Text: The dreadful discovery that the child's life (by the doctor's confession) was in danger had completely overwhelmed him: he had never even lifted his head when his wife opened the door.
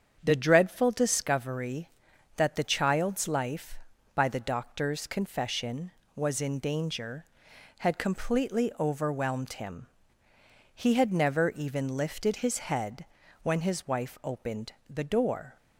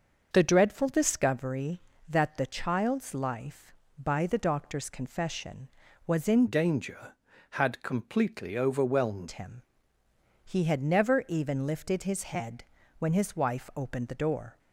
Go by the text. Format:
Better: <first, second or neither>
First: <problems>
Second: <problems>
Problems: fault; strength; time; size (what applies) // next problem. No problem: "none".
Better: first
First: starts louder than the rest; strong; until 1.2 s; 7.5 dB // pauses between "head" and "when"; at 13.0 s; 0.38 s long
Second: starts louder than the rest; until 1.3 s; 6.5 dB // changes voice from "danger" to "overwhelmed"; from 6.4 to 9.2 s; 2.8 s long // pauses between "head" and "when"; slight; at 12.6 s; 0.34 s long